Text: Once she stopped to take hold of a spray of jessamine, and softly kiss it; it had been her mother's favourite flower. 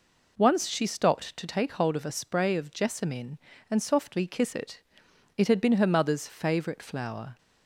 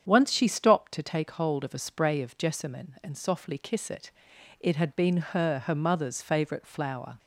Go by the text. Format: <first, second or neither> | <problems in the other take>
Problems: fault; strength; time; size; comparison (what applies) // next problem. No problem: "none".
first | starts louder than the rest; strong; until 1.0 s; 8 dB // says "her" twice; at 5.6 s